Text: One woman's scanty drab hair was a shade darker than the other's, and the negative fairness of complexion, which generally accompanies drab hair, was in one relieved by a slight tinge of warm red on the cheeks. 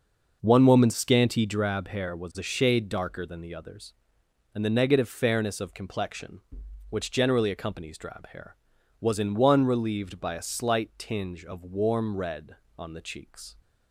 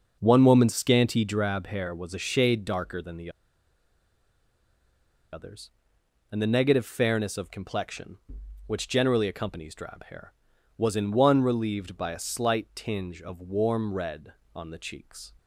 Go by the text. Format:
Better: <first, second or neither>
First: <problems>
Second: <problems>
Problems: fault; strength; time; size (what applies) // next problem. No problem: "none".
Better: first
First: none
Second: pauses between "the" and "other's"; strong; at 3.3 s; 2.0 s long